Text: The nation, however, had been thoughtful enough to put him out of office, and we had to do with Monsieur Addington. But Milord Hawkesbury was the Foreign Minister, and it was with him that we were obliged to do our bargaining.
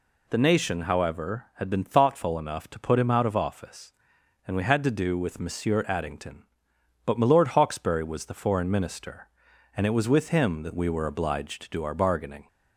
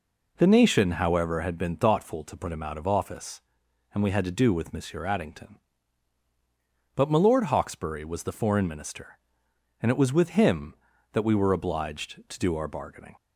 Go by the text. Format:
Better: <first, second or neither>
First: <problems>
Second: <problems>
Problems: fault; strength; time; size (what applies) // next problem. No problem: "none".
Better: first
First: none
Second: skips "enough"; at 2.2 s